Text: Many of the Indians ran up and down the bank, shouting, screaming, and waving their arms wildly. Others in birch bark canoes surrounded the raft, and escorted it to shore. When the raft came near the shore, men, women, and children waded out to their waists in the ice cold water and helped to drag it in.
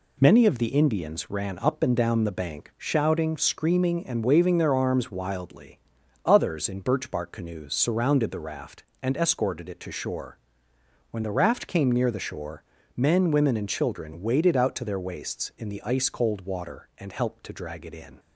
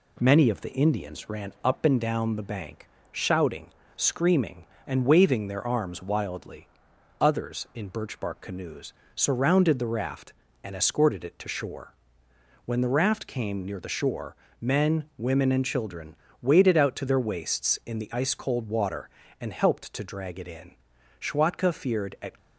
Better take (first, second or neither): first